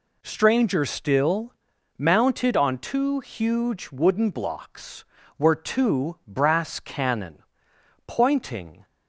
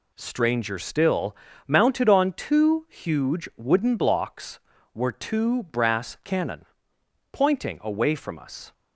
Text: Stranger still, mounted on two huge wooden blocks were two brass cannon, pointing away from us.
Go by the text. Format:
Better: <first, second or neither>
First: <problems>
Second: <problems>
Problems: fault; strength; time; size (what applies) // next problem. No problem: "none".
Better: second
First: stops before "away from us"; at 8.8 s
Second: none